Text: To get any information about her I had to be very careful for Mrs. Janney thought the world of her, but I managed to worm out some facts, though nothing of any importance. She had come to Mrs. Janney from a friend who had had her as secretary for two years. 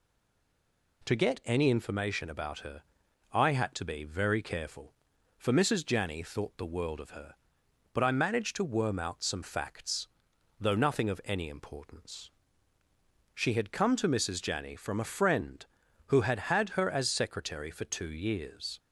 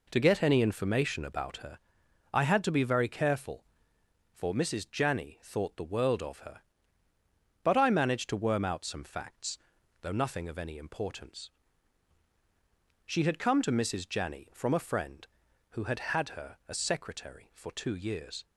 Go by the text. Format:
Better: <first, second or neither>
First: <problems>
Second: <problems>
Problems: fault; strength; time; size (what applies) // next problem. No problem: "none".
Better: second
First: stays silent before the first word; until 1.0 s; 1.0 s long // pauses between "her" and "I"; noticeable; at 2.8 s; 0.52 s long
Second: pauses between "her" and "I"; noticeable; at 1.7 s; 0.56 s long